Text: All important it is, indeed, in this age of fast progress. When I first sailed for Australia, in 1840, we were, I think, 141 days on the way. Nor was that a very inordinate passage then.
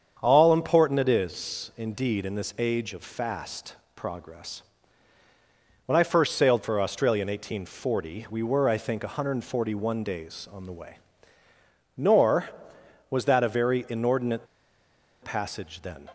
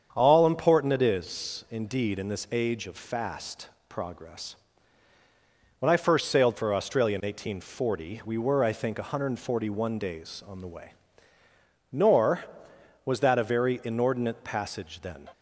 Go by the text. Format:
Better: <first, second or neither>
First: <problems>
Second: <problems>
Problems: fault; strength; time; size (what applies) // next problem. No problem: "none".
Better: second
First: starts louder than the rest; strong; until 1.2 s; 7.5 dB // pauses between "fast" and "progress"; slight; at 3.7 s; 0.18 s long // pauses between "inordinate" and "passage"; noticeable; at 14.4 s; 0.76 s long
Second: starts louder than the rest; strong; until 1.1 s; 7.5 dB // pauses between "fast" and "progress"; slight; at 3.6 s; 0.18 s long